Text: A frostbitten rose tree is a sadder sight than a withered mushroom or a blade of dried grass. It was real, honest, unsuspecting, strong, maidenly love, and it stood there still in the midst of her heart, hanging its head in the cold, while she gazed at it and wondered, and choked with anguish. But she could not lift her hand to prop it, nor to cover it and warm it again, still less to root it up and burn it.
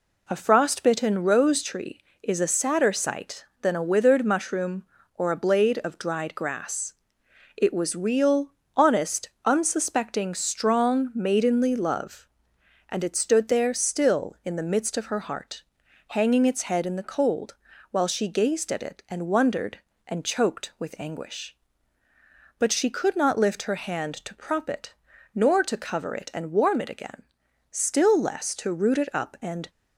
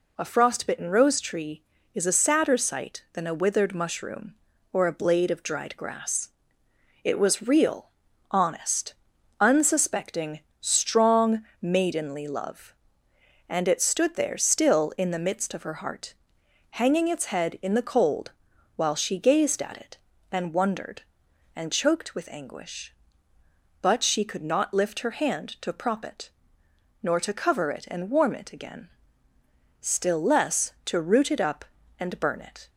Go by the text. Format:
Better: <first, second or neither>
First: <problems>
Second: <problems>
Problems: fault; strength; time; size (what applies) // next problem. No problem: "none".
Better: second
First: stops before "burn it"; at 29.6 s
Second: none